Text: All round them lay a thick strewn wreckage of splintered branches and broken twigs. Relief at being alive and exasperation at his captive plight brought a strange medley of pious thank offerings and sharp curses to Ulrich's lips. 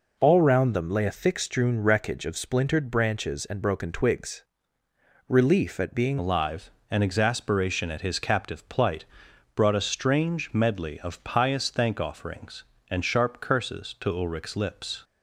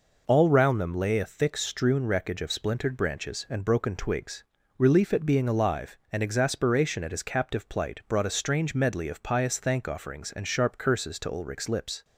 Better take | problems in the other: second | changes voice at "alive"; from 6.1 s on; 8.9 s long // pauses between "plight" and "brought"; noticeable; at 9.0 s; 0.52 s long

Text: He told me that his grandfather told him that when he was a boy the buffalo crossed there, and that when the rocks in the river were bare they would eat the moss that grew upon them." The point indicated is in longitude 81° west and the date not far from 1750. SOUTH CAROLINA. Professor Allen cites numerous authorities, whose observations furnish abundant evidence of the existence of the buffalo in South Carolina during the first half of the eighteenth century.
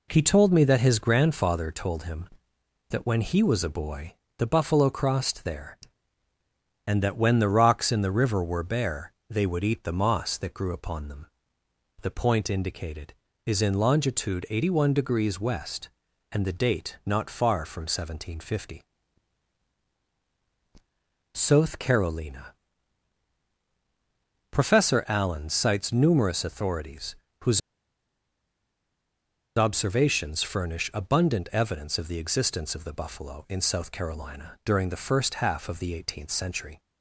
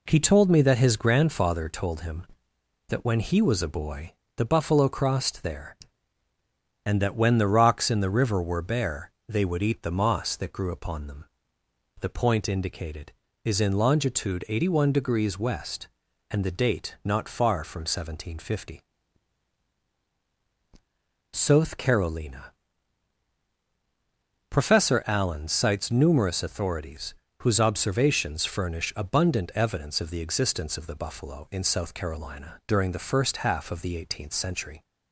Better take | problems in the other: second | pauses between "boy" and "the"; slight; at 4.1 s; 0.24 s long; slight in the second // pauses between "bare" and "they"; slight; at 9.1 s; 0.18 s long; slight in the second // pauses between "whose" and "observations"; strong; at 27.6 s; 1.9 s long

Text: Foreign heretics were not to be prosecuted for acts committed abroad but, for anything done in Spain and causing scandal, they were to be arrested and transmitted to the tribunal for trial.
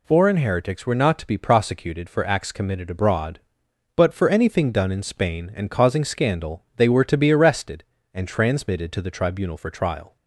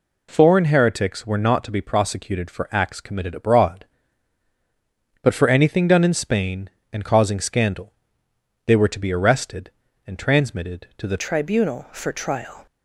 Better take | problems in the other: first | changes voice at "tribunal"; from 11.1 s on; 1.5 s long

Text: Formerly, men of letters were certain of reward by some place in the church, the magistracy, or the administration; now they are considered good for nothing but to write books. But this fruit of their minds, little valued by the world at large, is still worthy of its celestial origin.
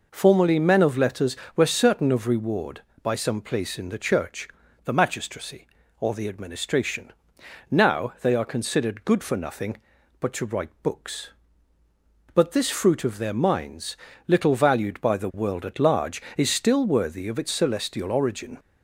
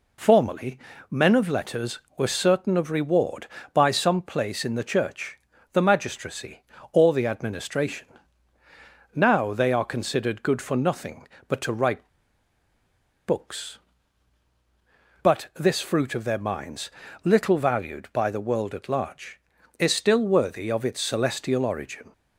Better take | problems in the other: first | pauses between "write" and "books"; at 12.0 s; 1.1 s long

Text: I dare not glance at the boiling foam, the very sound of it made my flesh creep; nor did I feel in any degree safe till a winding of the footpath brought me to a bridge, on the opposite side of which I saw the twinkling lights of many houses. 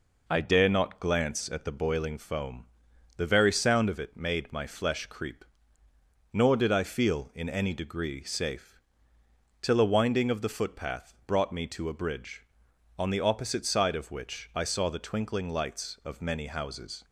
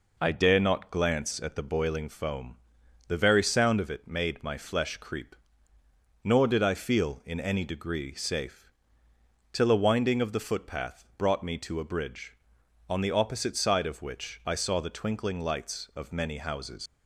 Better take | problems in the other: first | pauses between "safe" and "till"; noticeable; at 8.6 s; 0.84 s long; noticeable in the first // leaves "houses" unfinished; at 16.8 s; 95 ms

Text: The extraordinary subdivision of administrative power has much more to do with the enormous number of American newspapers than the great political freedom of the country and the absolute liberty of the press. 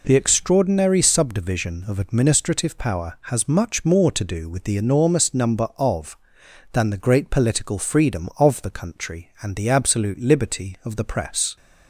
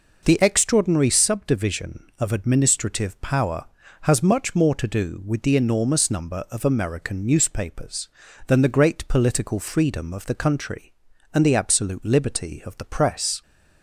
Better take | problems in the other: second | skips "American newspapers"; at 6.4 s

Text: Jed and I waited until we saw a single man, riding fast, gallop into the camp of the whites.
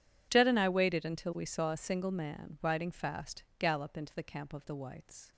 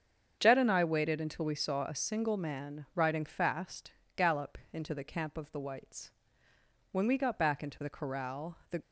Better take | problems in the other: first | starts louder than the rest; strong; until 1.4 s; 7.5 dB // goes on to say "When we got back into the corral the"; strong; from 6.9 s on; 1.8 s long

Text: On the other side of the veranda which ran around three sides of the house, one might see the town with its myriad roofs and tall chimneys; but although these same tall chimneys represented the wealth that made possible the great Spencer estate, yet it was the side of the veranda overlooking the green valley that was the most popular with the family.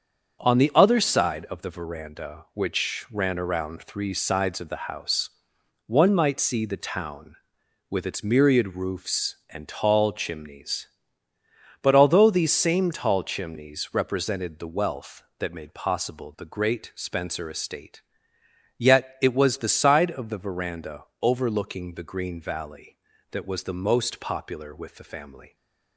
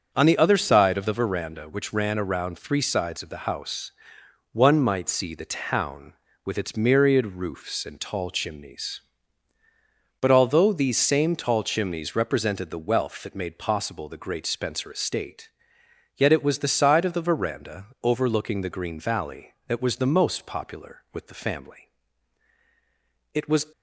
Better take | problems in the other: first | starts louder than the rest; until 1.1 s; 7 dB; also in the first // pauses between "veranda" and "overlooking"; slight; at 17.8 s; 0.18 s long; slight in the first // goes on to say "It was"; slight; from 23.3 s on; 0.32 s long

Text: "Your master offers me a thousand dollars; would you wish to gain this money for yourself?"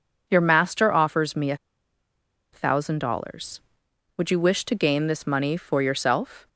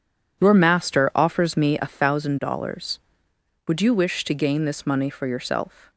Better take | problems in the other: second | pauses between "a" and "thousand"; noticeable; at 1.5 s; 0.97 s long

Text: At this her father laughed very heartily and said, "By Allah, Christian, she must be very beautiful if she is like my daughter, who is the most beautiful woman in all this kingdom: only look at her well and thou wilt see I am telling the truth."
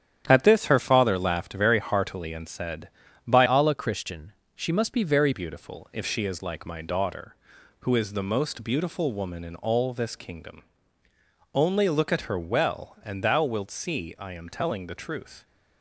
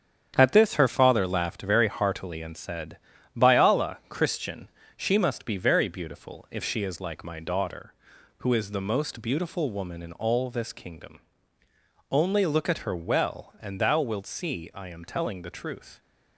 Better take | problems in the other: second | starts louder than the rest; strong; until 1.2 s; 9.5 dB; strong in the second // changes voice from "Allah" to "very"; from 3.4 to 5.3 s; 1.9 s long

